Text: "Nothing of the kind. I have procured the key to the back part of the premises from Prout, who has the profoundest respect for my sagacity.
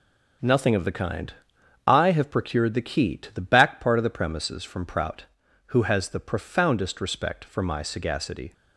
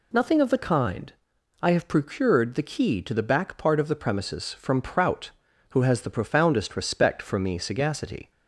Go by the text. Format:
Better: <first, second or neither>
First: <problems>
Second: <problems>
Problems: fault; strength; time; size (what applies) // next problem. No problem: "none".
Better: first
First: none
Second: says "me" for "my"; at 7.3 s